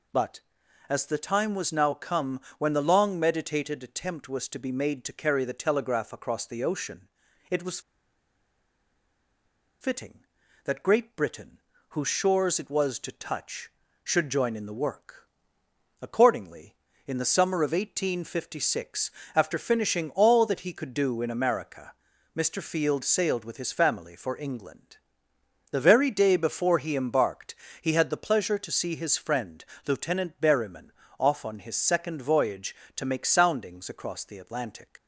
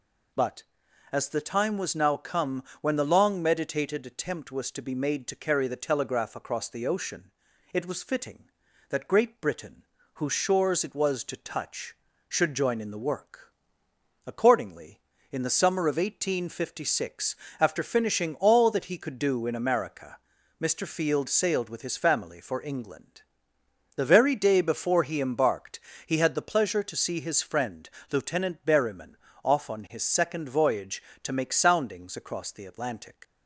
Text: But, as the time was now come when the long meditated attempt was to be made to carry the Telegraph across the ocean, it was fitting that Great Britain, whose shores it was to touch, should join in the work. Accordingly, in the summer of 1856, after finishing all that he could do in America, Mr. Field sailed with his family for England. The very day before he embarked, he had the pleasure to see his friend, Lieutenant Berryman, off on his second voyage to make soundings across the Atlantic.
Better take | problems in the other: second | pauses between "come" and "when"; slight; at 2.3 s; 0.18 s long; slight in the second // pauses between "was" and "fitting"; strong; at 7.7 s; 2.0 s long

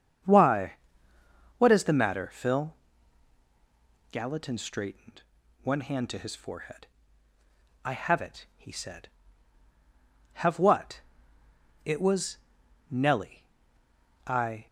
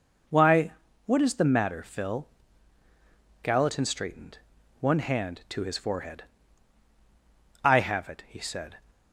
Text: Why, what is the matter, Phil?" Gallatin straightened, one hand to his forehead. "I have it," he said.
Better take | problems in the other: second | starts louder than the rest; strong; until 2.0 s; 7.5 dB // goes on to say "Have what It was Nellie I"; strong; from 10.3 s on; 4.3 s long

